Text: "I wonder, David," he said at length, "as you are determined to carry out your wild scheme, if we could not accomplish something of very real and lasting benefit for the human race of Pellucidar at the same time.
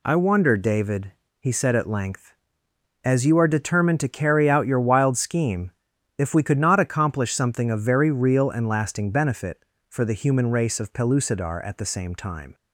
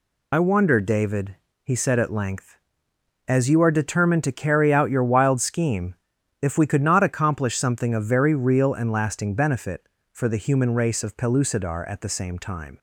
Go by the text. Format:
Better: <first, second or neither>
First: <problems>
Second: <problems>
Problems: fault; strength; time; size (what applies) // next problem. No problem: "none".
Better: first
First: none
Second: loses the start of "I"; at 0.3 s; 45 ms